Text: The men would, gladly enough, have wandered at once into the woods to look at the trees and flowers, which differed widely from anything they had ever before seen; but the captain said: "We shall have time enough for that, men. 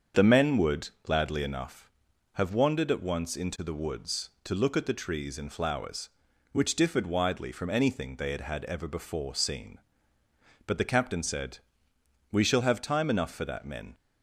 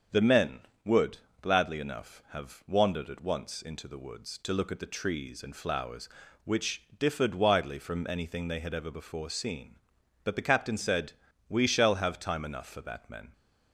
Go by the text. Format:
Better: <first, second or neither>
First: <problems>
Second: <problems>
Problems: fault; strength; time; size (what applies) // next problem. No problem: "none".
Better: second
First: starts louder than the rest; until 1.3 s; 7 dB // says "had" twice; at 8.4 s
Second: starts louder than the rest; strong; until 1.5 s; 7.5 dB